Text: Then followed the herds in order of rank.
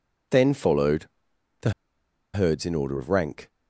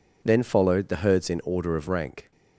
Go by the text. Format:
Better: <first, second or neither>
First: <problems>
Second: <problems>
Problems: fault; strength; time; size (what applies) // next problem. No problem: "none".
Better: second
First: pauses between "followed" and "the"; noticeable; at 1.0 s; 0.54 s long // pauses between "the" and "herds"; noticeable; at 1.7 s; 0.63 s long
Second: none